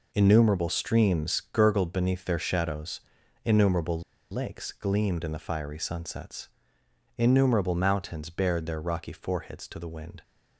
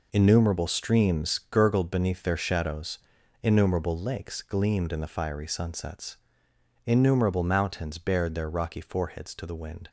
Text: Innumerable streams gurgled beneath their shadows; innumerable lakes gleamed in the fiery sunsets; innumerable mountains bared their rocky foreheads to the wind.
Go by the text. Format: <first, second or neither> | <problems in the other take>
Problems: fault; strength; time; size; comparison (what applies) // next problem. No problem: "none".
second | pauses between "innumerable" and "lakes"; slight; at 4.0 s; 0.31 s long